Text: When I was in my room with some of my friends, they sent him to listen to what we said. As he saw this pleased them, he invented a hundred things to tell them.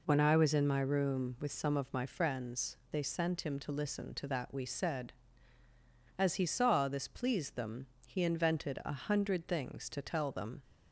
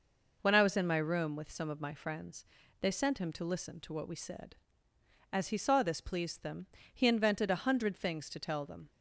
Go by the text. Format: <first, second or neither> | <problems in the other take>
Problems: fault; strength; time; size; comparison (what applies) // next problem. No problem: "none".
second | says "that" for "what"; at 4.2 s